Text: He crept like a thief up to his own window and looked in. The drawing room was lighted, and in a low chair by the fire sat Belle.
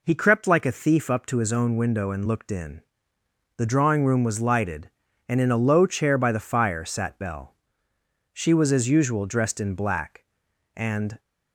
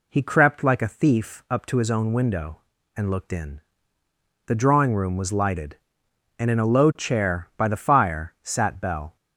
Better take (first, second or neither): second